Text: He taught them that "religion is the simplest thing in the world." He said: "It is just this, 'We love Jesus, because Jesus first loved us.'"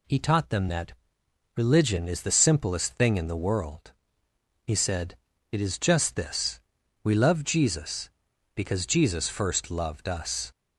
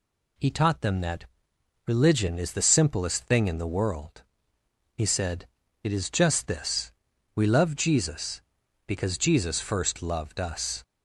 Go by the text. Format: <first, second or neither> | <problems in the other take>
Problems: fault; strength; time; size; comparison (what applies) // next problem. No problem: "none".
neither | pauses between "that" and "religion"; noticeable; the same in both